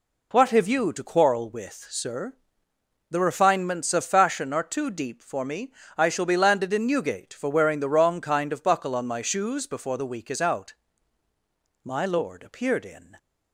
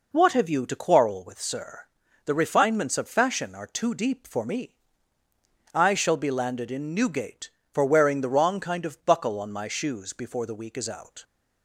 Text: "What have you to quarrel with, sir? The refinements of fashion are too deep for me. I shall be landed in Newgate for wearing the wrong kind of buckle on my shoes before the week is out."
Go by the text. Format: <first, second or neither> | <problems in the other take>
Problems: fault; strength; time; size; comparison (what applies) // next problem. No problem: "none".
second | goes on to say "My lord appeared in"; from 11.8 s on; 1.3 s long